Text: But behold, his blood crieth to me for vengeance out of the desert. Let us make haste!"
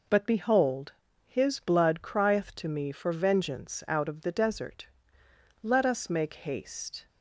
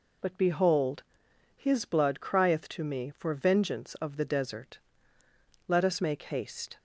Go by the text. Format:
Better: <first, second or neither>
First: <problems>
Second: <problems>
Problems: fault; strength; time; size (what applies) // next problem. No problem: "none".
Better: first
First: none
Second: skips "out"; at 3.9 s